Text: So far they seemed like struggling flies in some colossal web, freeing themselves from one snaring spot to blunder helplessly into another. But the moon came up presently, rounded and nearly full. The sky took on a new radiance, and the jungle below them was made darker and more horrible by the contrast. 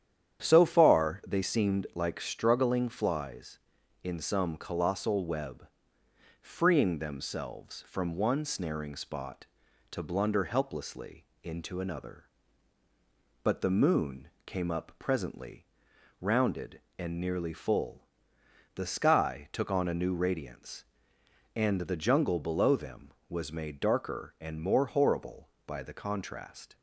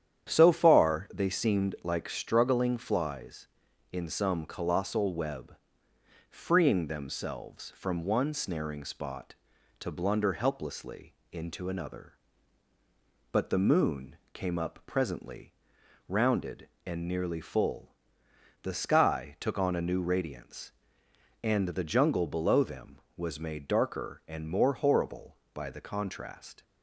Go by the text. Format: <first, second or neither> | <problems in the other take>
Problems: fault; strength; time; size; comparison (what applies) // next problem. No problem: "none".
neither | starts louder than the rest; strong; the same in both // pauses between "helplessly" and "into"; slight; the same in both // pauses between "moon" and "came"; slight; the same in both